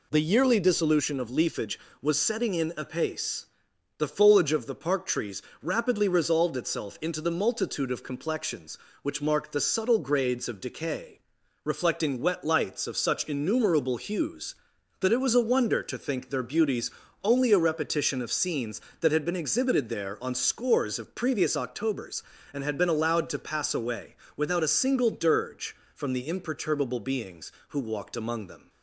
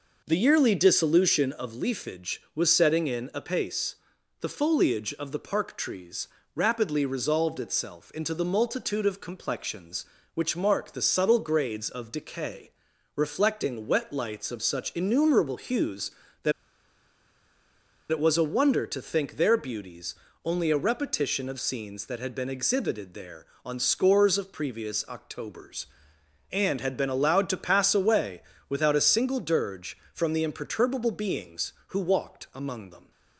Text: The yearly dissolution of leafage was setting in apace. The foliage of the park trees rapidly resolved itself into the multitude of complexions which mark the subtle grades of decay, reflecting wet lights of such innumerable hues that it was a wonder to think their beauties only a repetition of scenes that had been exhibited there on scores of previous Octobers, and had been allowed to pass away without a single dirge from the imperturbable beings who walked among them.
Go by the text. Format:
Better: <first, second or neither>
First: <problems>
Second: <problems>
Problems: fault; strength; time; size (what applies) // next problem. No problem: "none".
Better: first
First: pauses between "trees" and "rapidly"; slight; at 5.4 s; 0.18 s long // pauses between "beauties" and "only"; slight; at 16.8 s; 0.34 s long // pauses between "away" and "without"; slight; at 24.1 s; 0.22 s long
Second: pauses between "trees" and "rapidly"; slight; at 6.2 s; 0.26 s long // pauses between "that" and "it"; strong; at 16.5 s; 1.5 s long // pauses between "beauties" and "only"; slight; at 20.1 s; 0.30 s long // pauses between "away" and "without"; slight; at 28.4 s; 0.26 s long